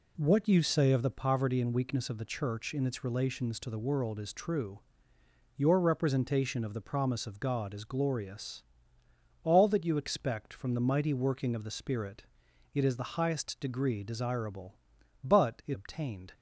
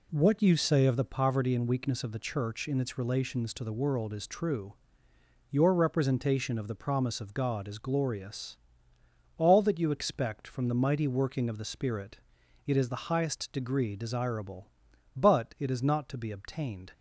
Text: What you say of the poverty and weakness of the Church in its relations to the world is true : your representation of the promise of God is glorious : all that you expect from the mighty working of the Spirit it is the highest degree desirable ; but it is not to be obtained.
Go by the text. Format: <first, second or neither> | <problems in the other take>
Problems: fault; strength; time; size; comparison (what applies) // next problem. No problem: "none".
second | pauses between "Spirit" and "it"; noticeable; at 12.2 s; 0.48 s long; noticeable in the second // skips "is not to be"; at 15.7 s